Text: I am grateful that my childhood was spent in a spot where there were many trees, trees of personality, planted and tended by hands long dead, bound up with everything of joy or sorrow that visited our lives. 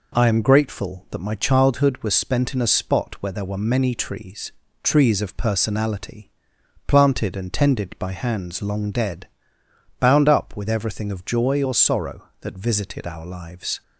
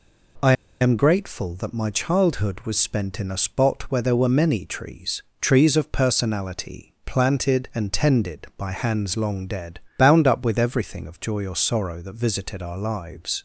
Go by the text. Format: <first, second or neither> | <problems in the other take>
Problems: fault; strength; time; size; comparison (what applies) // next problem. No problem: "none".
first | pauses between "I" and "am"; slight; at 0.5 s; 0.28 s long